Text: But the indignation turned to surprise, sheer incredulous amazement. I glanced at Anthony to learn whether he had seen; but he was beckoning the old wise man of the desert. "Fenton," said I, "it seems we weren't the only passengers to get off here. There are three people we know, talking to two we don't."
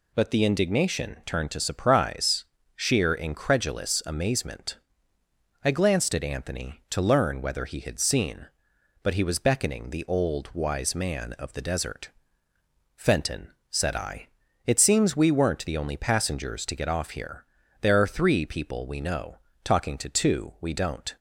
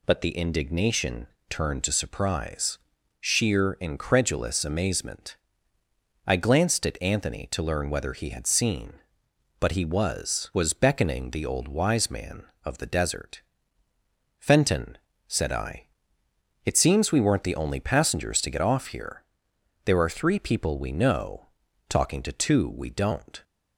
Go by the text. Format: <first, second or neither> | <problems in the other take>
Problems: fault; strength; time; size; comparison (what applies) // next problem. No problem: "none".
first | pauses between "indignation" and "turned"; slight; at 1.2 s; 0.22 s long // says "was" twice; at 10.5 s